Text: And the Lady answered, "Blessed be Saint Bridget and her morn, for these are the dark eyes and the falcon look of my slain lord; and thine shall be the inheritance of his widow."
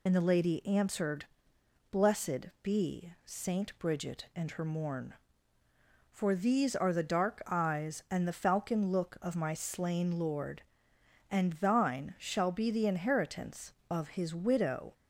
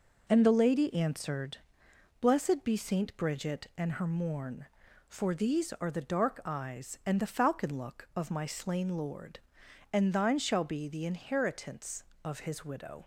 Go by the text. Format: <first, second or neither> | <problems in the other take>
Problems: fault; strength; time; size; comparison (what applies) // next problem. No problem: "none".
second | loses the start of "And"; at 0.0 s; 45 ms